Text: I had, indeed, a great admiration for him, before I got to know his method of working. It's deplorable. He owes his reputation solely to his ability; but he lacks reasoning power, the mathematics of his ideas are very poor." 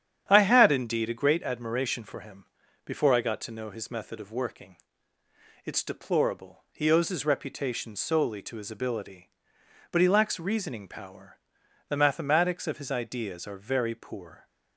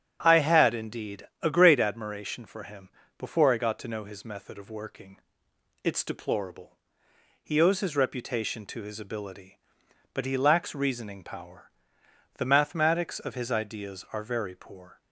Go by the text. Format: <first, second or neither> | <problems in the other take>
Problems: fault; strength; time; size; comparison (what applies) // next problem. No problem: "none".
first | starts louder than the rest; strong; until 1.2 s; 8.5 dB; strong in the first // skips "solely"; at 8.6 s